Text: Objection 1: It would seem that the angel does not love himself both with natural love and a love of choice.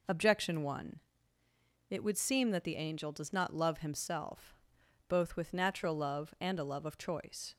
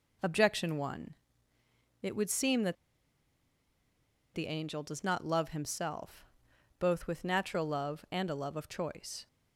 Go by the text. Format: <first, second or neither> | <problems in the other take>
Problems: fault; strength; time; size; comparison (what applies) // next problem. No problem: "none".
first | pauses between "that" and "the"; strong; at 2.7 s; 1.5 s long // pauses between "himself" and "both"; noticeable; at 6.2 s; 0.54 s long; noticeable in the first